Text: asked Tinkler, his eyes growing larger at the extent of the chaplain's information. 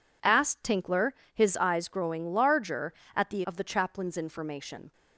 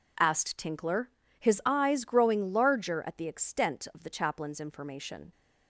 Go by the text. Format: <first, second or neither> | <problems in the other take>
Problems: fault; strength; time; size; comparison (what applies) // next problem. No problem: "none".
second | skips "extent"; at 3.4 s